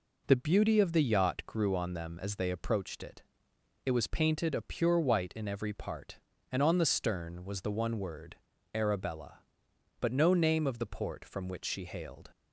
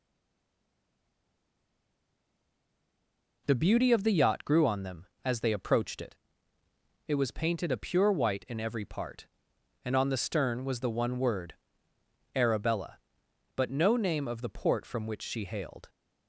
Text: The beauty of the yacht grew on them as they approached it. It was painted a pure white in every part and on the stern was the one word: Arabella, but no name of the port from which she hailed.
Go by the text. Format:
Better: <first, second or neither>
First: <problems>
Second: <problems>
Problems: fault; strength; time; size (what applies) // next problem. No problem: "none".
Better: first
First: none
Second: stays silent before the first word; strong; until 3.4 s; 3.4 s long